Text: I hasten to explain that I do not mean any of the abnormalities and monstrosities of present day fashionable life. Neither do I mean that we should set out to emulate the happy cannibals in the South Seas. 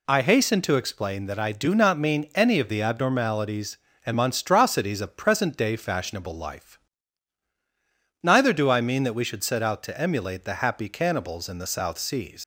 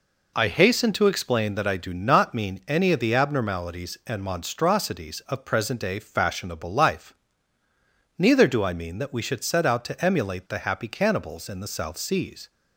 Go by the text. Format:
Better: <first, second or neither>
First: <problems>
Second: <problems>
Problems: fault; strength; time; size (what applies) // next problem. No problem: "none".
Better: second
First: leaves "Seas" unfinished; at 12.4 s; 105 ms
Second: none